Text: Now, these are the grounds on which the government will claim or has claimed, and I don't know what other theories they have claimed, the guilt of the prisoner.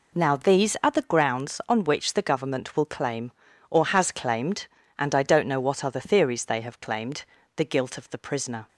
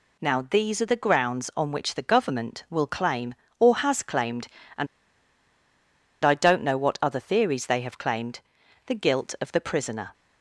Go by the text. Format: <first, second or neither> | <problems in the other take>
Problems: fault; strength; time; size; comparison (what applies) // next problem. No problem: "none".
first | pauses between "and" and "I"; strong; at 4.8 s; 1.3 s long